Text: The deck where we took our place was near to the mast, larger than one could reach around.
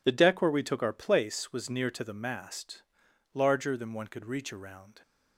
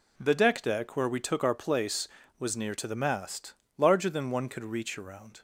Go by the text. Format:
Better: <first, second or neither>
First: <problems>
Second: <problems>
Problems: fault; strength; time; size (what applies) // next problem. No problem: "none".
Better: first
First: none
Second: says "deck" twice; at 0.6 s